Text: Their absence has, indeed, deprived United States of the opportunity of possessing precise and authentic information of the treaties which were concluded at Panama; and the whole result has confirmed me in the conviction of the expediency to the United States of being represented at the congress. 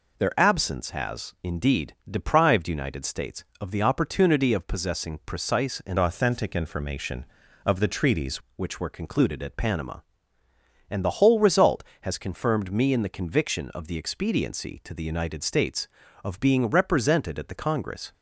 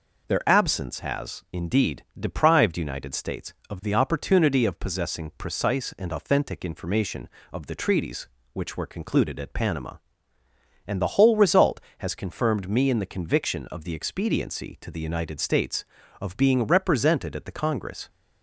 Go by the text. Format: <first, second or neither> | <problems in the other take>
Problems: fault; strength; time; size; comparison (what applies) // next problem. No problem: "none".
second | changes voice from "authentic" to "treaties"; from 5.9 to 8.3 s; 2.4 s long